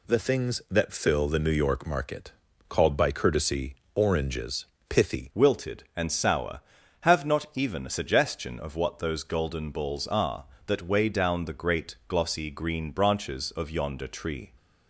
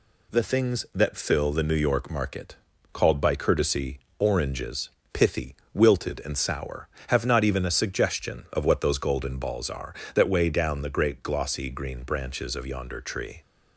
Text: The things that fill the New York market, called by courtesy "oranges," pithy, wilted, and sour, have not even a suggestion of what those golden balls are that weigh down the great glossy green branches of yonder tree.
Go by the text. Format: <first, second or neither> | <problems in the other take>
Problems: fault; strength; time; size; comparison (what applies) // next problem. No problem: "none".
second | pauses between "courtesy" and "oranges"; slight; at 3.7 s; 0.22 s long; slight in the second // changes voice at "wilted"; from 5.3 s on; 9.2 s long